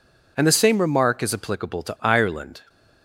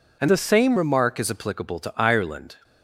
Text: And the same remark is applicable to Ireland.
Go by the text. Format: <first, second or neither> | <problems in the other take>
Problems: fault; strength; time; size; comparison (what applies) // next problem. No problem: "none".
first | changes voice from "the" to "same"; from 0.2 to 0.7 s; 0.5 s long